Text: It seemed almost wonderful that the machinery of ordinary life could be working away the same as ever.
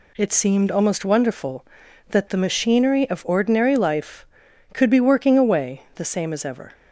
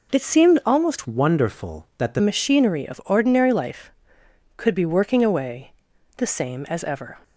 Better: first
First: none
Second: changes voice from "wonderful" to "the"; from 1.0 to 2.2 s; 1.2 s long // pauses between "away" and "the"; noticeable; at 5.7 s; 0.46 s long

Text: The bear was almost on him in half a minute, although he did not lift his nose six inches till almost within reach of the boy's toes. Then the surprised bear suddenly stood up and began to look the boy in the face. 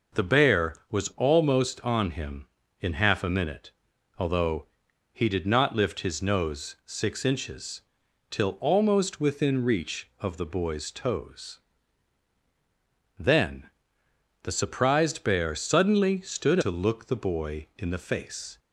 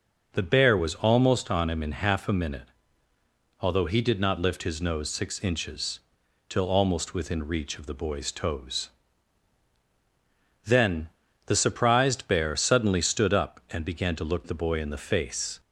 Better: second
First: pauses between "although" and "he"; at 4.6 s; 0.44 s long // pauses between "inches" and "till"; noticeable; at 7.8 s; 0.48 s long // pauses between "Then" and "the"; noticeable; at 13.6 s; 0.74 s long // skips "up and began"; at 16.5 s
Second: pauses between "inches" and "till"; noticeable; at 5.9 s; 0.48 s long // pauses between "Then" and "the"; at 11.0 s; 0.38 s long

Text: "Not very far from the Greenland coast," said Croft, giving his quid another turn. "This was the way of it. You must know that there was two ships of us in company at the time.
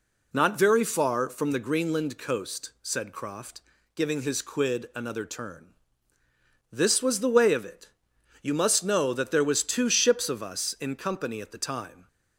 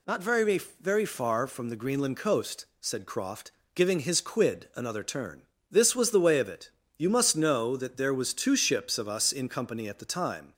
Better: first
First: none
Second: says "very" twice; at 0.7 s

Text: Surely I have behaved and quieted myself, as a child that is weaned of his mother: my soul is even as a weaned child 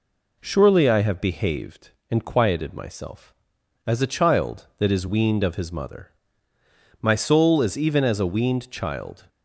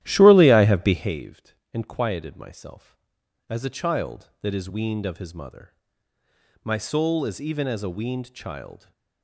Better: first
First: none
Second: starts louder than the rest; strong; until 1.2 s; 13 dB

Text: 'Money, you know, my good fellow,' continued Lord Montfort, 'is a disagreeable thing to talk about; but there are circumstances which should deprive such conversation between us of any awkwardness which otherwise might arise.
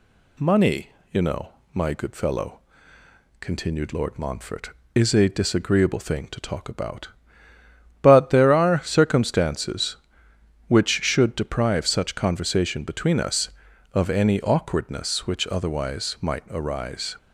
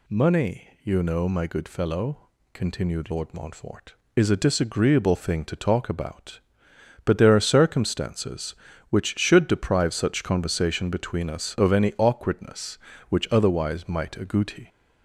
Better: first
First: none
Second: says "agouti" for "arise"; at 14.1 s

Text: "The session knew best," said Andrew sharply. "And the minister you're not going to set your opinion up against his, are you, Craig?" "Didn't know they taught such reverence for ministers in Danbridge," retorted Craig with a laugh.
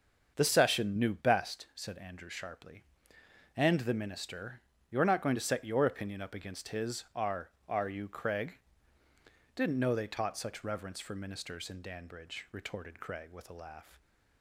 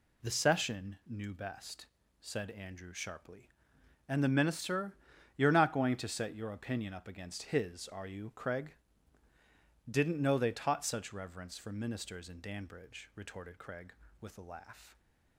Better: second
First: starts louder than the rest; until 1.3 s; 6.5 dB // pauses between "minister" and "you're"; slight; at 4.6 s; 0.30 s long // says "are" twice; at 7.6 s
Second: pauses between "minister" and "you're"; at 4.9 s; 0.40 s long

